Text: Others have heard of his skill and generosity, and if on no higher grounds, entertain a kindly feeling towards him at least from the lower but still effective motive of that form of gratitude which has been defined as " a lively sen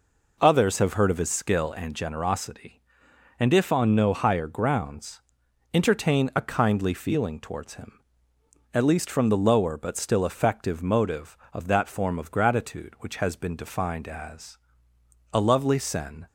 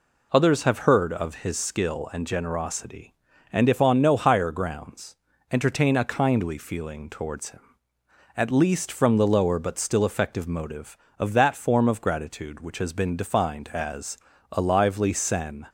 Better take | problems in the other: second | says "lovely" for "lively"; at 15.4 s

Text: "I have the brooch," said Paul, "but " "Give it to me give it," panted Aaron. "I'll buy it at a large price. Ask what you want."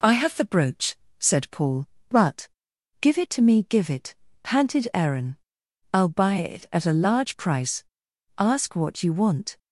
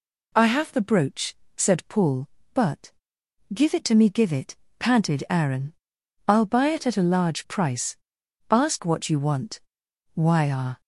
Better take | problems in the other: first | goes on to say "Why are"; noticeable; from 10.1 s on; 0.66 s long

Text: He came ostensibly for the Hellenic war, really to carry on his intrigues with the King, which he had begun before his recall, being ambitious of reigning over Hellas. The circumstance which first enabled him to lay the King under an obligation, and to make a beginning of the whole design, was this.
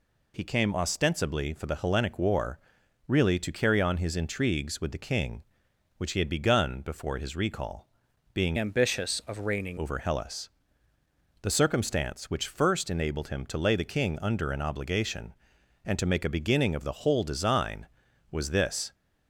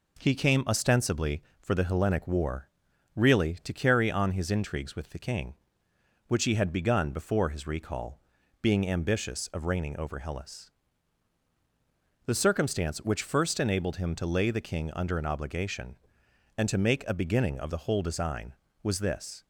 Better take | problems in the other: second | changes voice from "ambitious" to "reigning"; from 8.5 to 9.7 s; 1.2 s long

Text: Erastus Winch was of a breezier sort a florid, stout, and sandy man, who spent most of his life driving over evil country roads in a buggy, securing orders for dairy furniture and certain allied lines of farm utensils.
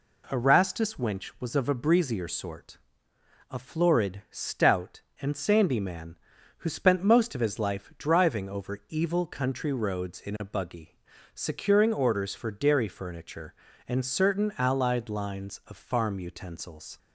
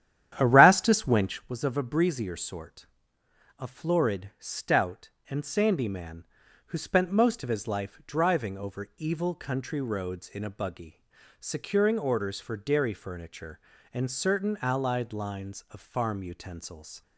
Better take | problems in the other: first | starts louder than the rest; strong; until 1.6 s; 10.5 dB // pauses between "sort" and "a"; noticeable; at 2.8 s; 0.72 s long; noticeable in the first

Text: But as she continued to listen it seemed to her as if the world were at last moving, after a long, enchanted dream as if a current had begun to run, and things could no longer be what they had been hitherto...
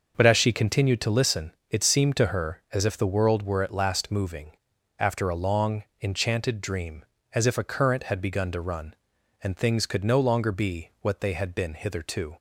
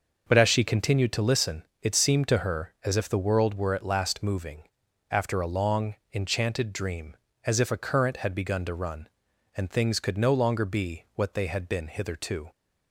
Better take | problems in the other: neither | pauses between "listen" and "it"; slight; the same in both

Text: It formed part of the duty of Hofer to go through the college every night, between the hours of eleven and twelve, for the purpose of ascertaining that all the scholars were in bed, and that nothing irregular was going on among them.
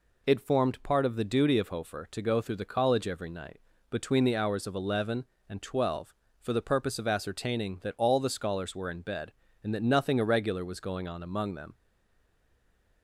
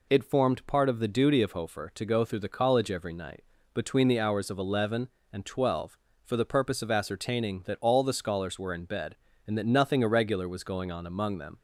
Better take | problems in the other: second | stays silent after the last word; noticeable; from 11.7 s on; 1.3 s long

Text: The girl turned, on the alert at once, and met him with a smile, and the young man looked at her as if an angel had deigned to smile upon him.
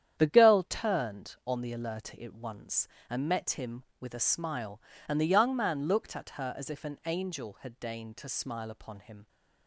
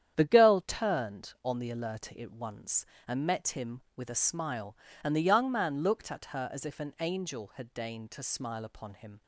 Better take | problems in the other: neither | starts louder than the rest; strong; the same in both

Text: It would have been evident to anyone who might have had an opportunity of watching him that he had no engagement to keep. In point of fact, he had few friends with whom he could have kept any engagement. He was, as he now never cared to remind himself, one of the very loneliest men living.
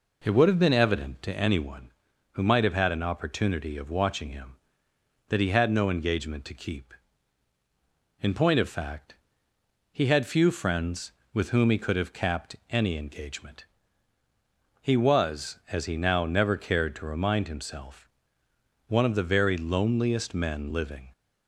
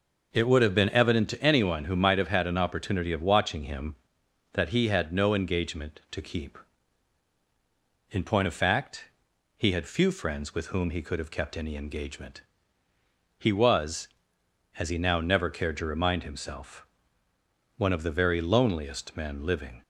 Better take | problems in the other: second | says "capped" for "kept"; at 12.1 s

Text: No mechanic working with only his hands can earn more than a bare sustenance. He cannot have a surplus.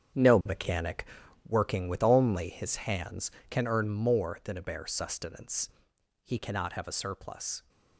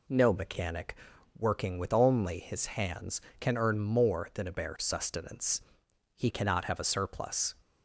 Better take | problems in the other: second | gets quieter; strong; throughout; 9.5 dB // pauses between "mechanic" and "working"; at 1.0 s; 0.42 s long; also in the second

